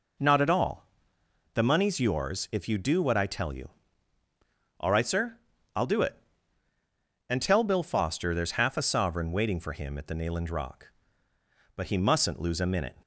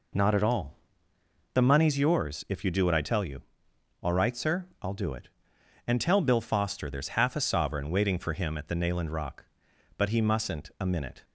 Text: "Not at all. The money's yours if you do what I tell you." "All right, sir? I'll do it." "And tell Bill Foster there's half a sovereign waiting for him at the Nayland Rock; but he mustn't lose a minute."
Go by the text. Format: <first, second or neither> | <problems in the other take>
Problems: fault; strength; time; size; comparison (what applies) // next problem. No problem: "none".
first | skips "lose"; at 10.7 s